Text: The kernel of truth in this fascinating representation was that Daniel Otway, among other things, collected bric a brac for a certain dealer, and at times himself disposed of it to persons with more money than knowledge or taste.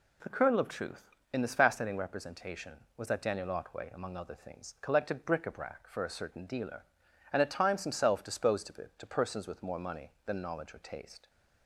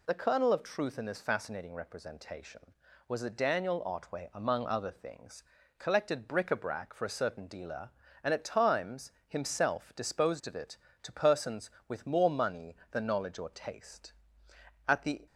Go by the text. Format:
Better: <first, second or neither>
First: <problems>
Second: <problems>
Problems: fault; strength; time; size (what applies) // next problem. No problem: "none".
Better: first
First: none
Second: pauses between "times" and "himself"; slight; at 9.1 s; 0.16 s long // goes on to say "At the"; slight; from 14.8 s on; 0.38 s long